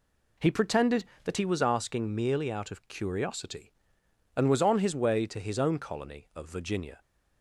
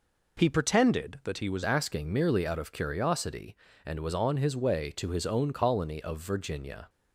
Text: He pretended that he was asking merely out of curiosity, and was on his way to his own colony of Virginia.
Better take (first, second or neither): first